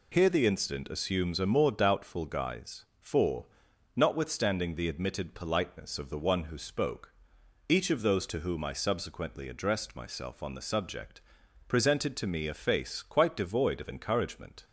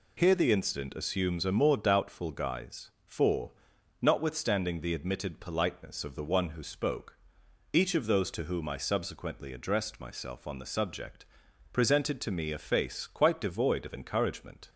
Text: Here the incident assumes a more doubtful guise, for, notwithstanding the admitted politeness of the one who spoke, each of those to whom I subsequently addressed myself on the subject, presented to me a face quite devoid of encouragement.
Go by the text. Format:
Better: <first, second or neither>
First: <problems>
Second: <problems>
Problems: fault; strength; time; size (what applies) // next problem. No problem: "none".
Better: neither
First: none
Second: none